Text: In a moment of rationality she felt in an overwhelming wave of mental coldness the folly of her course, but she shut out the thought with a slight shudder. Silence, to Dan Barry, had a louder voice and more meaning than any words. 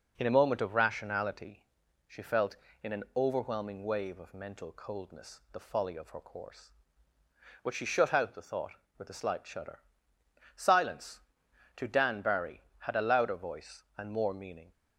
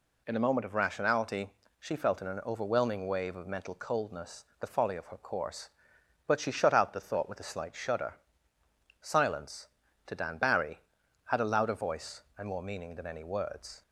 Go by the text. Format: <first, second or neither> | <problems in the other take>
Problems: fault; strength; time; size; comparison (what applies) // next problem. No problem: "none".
second | pauses between "rationality" and "she"; at 1.6 s; 0.42 s long; slight in the second // stops before "than any words"; at 14.7 s